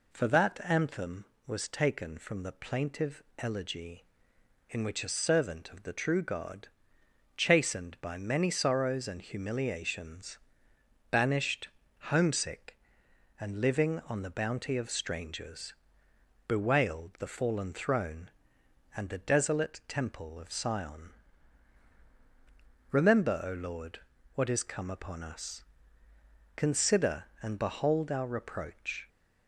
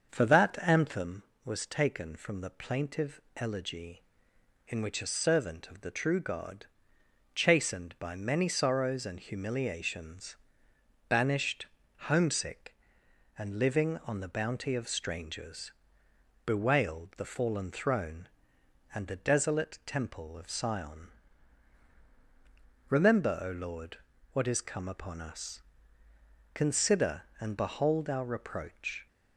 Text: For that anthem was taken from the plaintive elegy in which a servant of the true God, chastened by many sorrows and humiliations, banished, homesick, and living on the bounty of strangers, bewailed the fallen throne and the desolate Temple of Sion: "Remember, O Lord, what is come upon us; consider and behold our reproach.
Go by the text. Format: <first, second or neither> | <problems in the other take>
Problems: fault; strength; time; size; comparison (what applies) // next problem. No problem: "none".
first | starts louder than the rest; until 1.1 s; 6.5 dB // pauses between "plaintive" and "elegy"; slight; at 3.2 s; 0.16 s long; slight in the first